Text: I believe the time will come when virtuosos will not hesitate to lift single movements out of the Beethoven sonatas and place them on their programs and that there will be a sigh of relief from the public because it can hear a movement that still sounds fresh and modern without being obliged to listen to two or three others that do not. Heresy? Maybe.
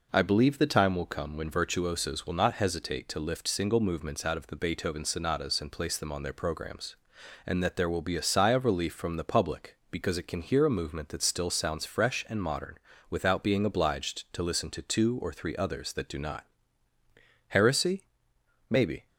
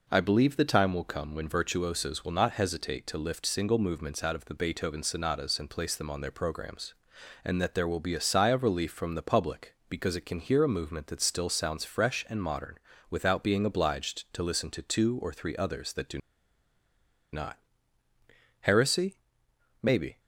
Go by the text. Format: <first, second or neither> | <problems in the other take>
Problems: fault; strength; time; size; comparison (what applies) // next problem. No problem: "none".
first | pauses between "modern" and "without"; slight; at 12.7 s; 0.32 s long; slight in the first // pauses between "do" and "not"; at 16.1 s; 1.1 s long